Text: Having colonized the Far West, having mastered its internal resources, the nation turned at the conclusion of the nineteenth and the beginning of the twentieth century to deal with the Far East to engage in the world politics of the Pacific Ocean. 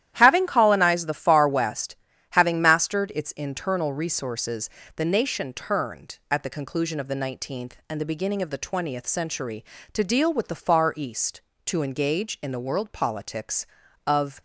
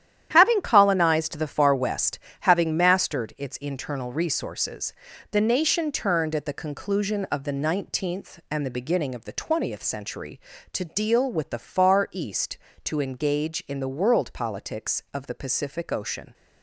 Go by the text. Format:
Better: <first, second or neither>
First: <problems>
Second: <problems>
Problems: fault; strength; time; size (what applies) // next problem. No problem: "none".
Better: second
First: starts louder than the rest; strong; until 1.1 s; 12 dB // stops before "the Pacific Ocean"; at 14.3 s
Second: starts louder than the rest; strong; until 1.3 s; 10.5 dB